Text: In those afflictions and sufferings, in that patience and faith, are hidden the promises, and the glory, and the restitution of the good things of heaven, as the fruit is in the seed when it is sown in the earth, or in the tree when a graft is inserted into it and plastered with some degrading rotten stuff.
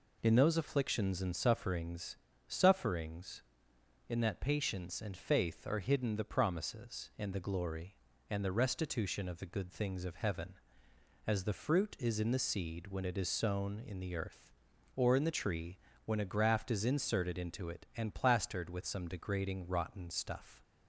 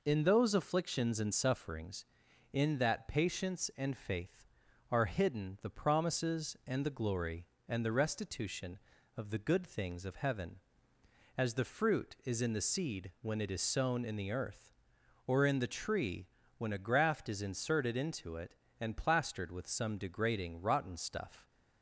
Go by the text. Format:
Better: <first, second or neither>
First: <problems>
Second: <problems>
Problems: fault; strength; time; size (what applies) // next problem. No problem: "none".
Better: second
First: says "sufferings" twice; at 2.4 s // pauses between "tree" and "when"; slight; at 15.7 s; 0.30 s long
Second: pauses between "tree" and "when"; slight; at 16.2 s; 0.32 s long